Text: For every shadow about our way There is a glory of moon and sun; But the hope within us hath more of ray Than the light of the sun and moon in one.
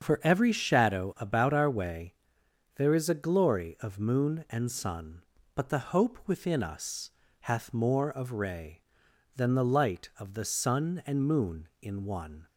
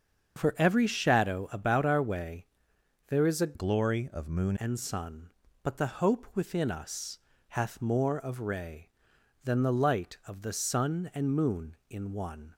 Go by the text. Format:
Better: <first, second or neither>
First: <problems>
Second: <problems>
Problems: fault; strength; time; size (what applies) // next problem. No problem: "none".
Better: first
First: starts louder than the rest; until 1.0 s; 7 dB // pauses between "way" and "There"; noticeable; at 2.1 s; 0.62 s long // pauses between "us" and "hath"; slight; at 7.0 s; 0.30 s long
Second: starts louder than the rest; until 1.4 s; 7 dB // pauses between "way" and "There"; noticeable; at 2.4 s; 0.62 s long // changes voice from "glory" to "moon"; from 3.5 to 4.5 s; 1.0 s long // pauses between "us" and "hath"; slight; at 7.1 s; 0.30 s long